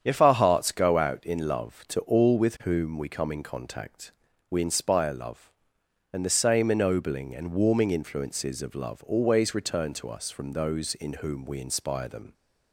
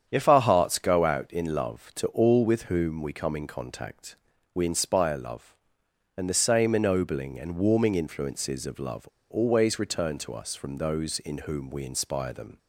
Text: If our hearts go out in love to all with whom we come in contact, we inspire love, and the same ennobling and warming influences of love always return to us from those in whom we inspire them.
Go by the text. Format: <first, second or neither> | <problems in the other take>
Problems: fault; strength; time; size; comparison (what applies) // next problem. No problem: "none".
first | starts louder than the rest; strong; until 1.1 s; 8 dB; strong in the first // pauses between "love" and "always"; slight; at 9.0 s; 0.25 s long